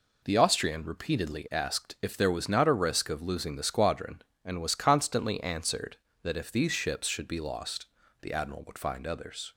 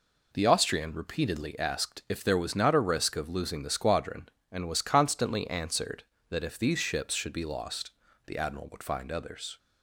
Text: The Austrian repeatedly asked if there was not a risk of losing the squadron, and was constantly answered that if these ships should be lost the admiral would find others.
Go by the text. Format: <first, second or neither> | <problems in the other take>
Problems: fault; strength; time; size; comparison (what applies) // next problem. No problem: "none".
neither | pauses between "lost" and "the"; slight; the same in both